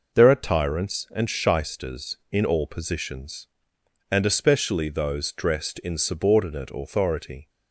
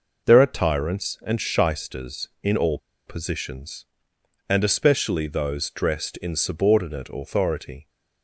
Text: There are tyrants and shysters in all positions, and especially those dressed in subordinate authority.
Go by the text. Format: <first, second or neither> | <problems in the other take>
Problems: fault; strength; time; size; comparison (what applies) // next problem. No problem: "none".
first | pauses between "all" and "positions"; slight; at 2.7 s; 0.29 s long